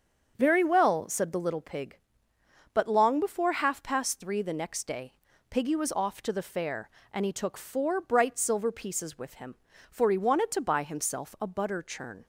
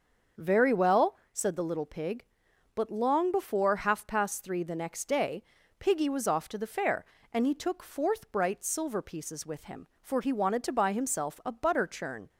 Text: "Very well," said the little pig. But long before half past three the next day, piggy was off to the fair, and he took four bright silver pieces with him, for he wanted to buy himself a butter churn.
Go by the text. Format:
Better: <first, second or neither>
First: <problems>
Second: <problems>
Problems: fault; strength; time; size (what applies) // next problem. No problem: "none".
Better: first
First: starts louder than the rest; until 1.3 s; 7 dB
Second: starts louder than the rest; until 1.5 s; 6.5 dB // says "fourth" for "four"; at 7.8 s